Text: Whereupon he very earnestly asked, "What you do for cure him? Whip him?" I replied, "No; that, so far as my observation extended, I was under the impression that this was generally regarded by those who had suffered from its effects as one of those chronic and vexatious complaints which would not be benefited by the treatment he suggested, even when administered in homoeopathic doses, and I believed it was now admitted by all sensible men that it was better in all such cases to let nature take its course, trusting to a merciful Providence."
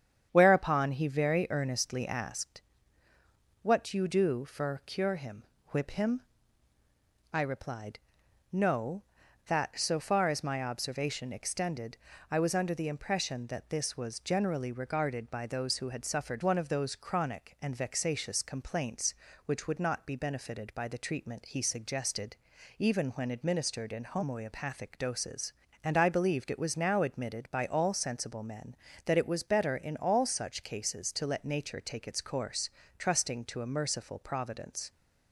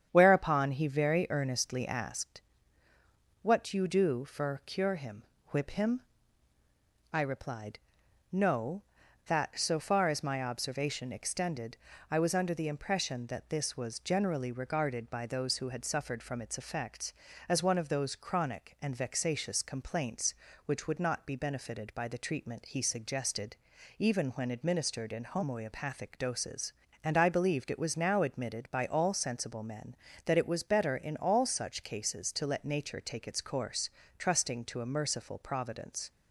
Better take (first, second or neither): second